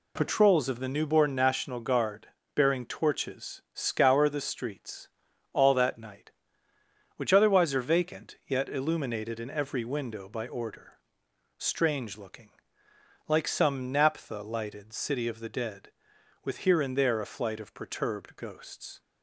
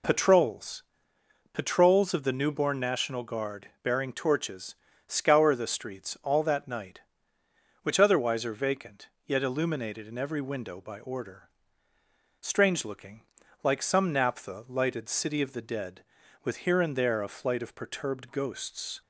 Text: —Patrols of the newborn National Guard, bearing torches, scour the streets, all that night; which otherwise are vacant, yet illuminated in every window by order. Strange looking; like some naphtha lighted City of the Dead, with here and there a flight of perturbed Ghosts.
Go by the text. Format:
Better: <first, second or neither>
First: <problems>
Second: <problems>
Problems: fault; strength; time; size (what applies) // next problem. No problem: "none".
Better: first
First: none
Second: says "Patrols" twice; at 1.5 s